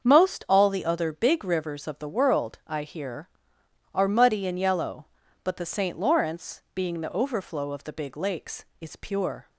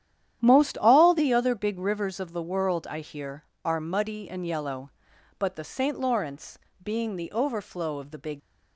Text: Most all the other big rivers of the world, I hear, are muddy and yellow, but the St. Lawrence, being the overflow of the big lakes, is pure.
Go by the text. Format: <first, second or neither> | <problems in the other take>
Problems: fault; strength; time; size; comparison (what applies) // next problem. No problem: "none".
first | starts louder than the rest; strong; until 1.4 s; 10.5 dB; also in the first // stops before "lakes is pure"; at 8.3 s